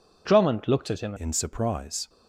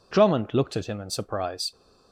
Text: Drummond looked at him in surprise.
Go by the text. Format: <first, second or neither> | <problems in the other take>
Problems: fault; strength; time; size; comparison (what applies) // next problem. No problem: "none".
second | changes voice at "in"; from 1.1 s on; 0.9 s long